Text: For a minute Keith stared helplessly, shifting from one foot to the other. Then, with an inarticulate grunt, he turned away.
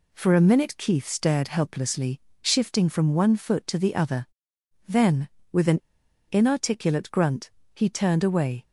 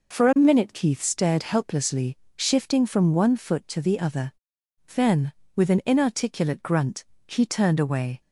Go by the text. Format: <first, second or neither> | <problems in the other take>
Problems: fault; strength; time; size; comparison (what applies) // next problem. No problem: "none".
second | pauses between "an" and "inarticulate"; noticeable; at 5.8 s; 0.49 s long